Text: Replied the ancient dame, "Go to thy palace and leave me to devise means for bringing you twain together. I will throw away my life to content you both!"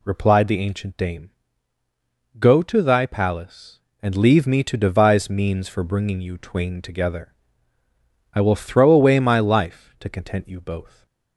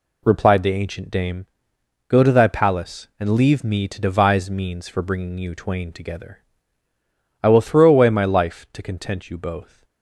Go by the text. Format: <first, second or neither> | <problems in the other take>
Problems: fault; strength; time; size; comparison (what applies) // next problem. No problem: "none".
neither | none